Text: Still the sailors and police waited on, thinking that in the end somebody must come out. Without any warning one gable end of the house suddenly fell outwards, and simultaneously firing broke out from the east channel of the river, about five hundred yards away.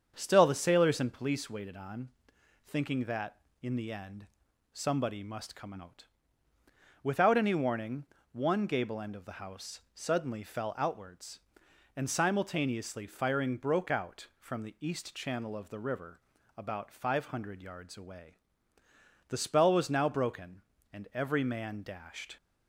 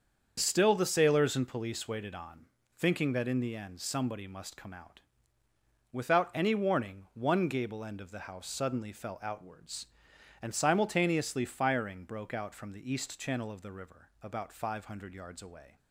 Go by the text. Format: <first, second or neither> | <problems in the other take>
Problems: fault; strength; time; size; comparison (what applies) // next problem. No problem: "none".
second | starts louder than the rest; strong; until 1.1 s; 7.5 dB; also in the second // pauses between "end" and "somebody"; noticeable; at 4.2 s; 0.46 s long // pauses between "warning" and "one"; slight; at 8.0 s; 0.26 s long // goes on to say "The spell was now broken and every man dashed"; strong; from 19.2 s on; 3.0 s long